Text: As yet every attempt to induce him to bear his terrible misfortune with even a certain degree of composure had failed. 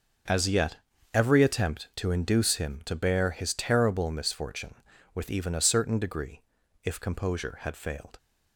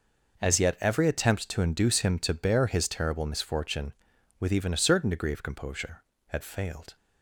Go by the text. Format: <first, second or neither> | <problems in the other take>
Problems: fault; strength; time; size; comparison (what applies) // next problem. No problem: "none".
second | starts louder than the rest; until 1.6 s; 6.5 dB // pauses between "yet" and "every"; at 0.7 s; 0.38 s long // says "if" for "of"; at 6.8 s